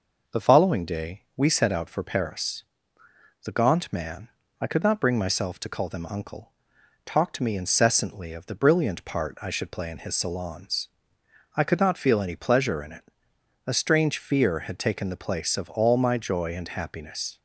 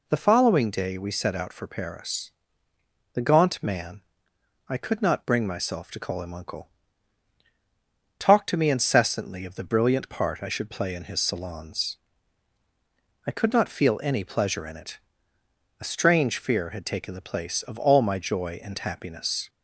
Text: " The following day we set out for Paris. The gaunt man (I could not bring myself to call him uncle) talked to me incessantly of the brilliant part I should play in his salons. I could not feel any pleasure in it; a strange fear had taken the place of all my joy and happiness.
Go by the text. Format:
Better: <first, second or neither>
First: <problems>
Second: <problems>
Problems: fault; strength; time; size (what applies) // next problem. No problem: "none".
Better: second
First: says "them" for "him"; at 5.8 s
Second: none